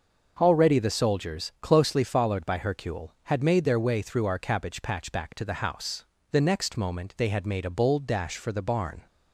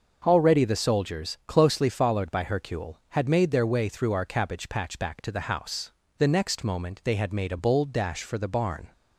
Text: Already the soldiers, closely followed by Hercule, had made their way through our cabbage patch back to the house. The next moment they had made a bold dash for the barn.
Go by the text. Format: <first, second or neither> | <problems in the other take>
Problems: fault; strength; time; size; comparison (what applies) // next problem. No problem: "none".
neither | starts louder than the rest; the same in both